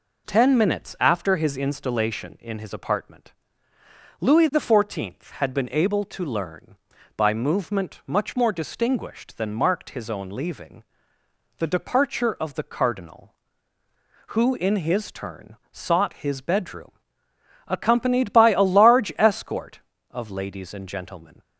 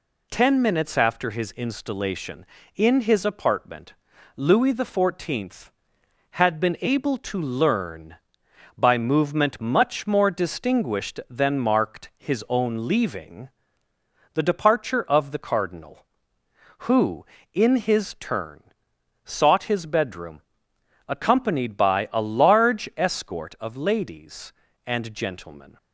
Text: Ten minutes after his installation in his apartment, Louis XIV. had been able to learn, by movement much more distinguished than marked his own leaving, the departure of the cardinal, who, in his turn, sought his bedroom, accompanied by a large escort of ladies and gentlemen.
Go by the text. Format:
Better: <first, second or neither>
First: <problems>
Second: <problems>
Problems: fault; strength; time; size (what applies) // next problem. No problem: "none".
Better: neither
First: none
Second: none